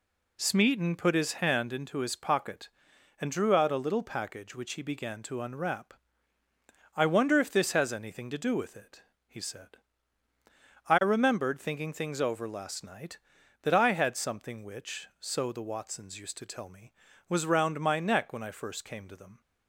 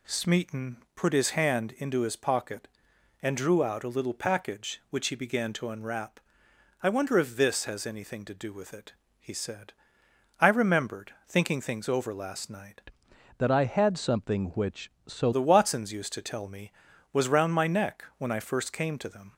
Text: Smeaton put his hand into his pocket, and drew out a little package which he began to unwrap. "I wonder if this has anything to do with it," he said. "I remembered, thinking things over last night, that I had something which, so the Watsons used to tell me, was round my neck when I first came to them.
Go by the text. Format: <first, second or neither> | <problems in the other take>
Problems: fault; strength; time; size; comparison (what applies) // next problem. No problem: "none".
first | pauses between "Smeaton" and "put"; slight; at 0.7 s; 0.18 s long // changes voice from "that" to "so"; from 13.3 to 15.3 s; 2.0 s long